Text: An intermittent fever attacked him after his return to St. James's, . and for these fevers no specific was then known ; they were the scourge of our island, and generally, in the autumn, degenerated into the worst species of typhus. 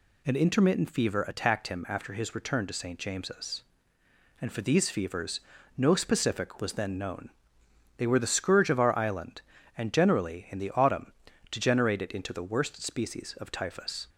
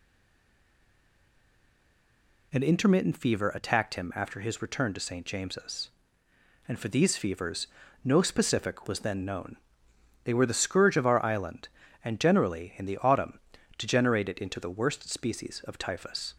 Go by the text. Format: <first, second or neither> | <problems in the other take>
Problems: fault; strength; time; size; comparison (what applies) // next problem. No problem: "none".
first | stays silent before the first word; until 2.5 s; 2.5 s long // pauses between "fevers" and "no"; at 7.6 s; 0.38 s long; also in the first